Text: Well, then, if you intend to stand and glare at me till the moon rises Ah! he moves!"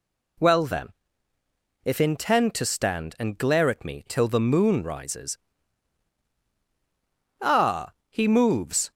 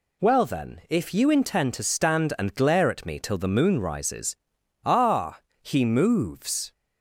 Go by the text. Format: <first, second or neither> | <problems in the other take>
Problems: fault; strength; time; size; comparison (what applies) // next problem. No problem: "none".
second | skips "you"; at 2.0 s // pauses between "rises" and "Ah"; strong; at 5.3 s; 2.0 s long; noticeable in the second